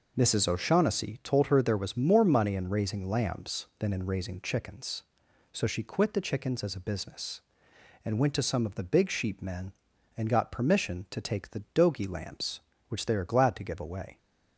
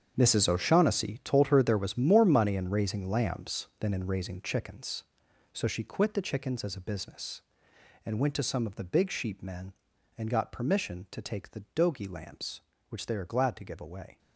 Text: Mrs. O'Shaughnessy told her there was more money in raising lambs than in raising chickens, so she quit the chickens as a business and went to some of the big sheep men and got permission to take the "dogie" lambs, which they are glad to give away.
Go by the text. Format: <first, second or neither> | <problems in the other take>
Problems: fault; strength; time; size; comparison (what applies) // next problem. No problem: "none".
first | gets quieter; strong; throughout; 13 dB